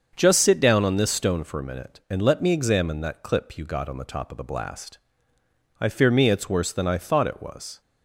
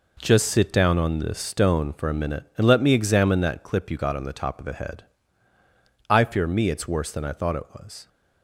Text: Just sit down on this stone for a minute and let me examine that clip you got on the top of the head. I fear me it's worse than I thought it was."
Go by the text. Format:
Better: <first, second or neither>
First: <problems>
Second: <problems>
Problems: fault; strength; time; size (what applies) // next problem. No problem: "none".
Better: second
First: starts louder than the rest; until 1.1 s; 6.5 dB // says "blast" for "head"; at 4.4 s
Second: none